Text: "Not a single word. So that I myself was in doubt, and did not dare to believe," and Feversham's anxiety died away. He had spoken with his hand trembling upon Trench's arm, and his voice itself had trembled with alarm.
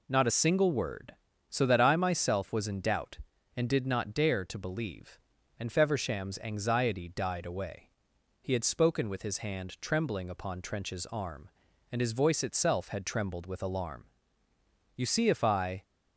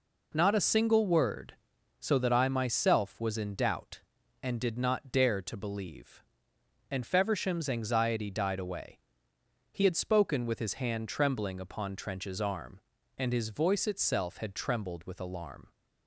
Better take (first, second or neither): second